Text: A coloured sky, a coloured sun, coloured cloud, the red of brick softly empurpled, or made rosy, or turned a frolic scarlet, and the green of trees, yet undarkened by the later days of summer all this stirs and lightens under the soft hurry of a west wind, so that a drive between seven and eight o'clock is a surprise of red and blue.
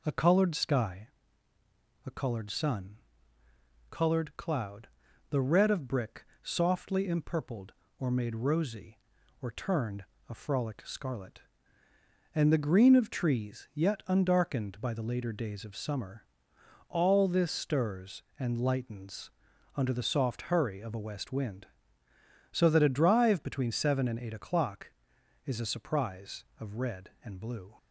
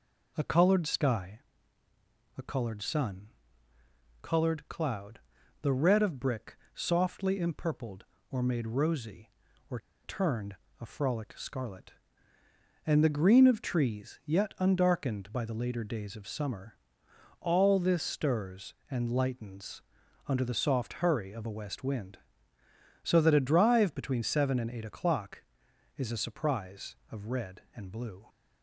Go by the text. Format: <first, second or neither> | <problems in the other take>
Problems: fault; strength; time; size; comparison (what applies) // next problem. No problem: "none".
first | pauses between "brick" and "softly"; slight; at 6.5 s; 0.18 s long; slight in the first // pauses between "or" and "turned"; slight; at 9.7 s; 0.26 s long // pauses between "turned" and "a"; slight; at 10.5 s; 0.26 s long; slight in the first // pauses between "summer" and "all"; noticeable; at 16.7 s; 0.62 s long; noticeable in the first // pauses between "lightens" and "under"; at 19.8 s; 0.44 s long; also in the first